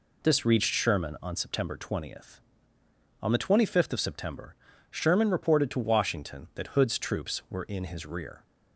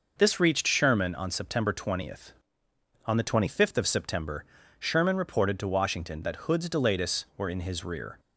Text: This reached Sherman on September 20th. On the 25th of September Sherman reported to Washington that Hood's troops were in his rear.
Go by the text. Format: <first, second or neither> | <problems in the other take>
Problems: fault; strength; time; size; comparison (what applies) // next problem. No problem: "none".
first | pauses between "September" and "Sherman"; slight; at 4.4 s; 0.34 s long; slight in the first // says "delatus" for "troops"; at 6.6 s